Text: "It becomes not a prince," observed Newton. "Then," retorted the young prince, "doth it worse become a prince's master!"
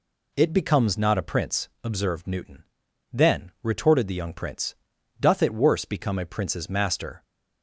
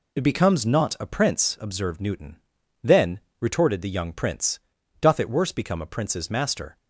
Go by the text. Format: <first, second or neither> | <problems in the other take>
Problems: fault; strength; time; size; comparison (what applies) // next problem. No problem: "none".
neither | none